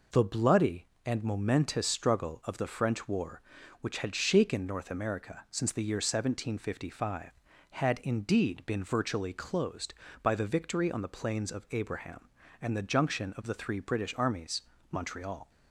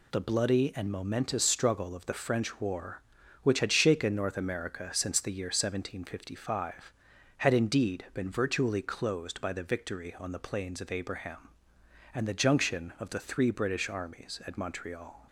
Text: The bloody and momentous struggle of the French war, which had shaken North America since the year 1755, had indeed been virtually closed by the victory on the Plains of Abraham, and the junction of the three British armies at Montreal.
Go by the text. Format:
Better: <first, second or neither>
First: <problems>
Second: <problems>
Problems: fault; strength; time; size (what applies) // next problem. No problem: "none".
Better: second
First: skips "at"; at 14.7 s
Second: none